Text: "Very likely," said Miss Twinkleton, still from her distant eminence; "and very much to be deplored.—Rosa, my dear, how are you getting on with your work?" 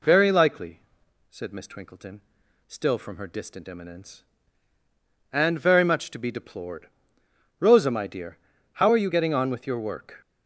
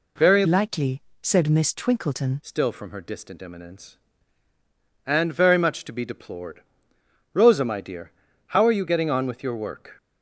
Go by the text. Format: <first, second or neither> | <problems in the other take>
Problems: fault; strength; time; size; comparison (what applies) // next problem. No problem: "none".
first | changes voice from "likely" to "Twinkleton"; from 0.4 to 2.4 s; 2.0 s long